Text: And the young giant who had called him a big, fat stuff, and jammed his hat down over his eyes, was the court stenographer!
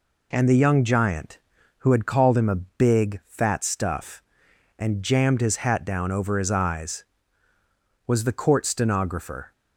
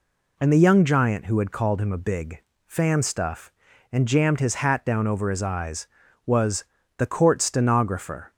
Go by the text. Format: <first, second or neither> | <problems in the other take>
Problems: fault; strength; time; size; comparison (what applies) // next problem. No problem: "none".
first | says "fan" for "fat"; at 2.6 s // pauses between "was" and "the"; slight; at 6.6 s; 0.34 s long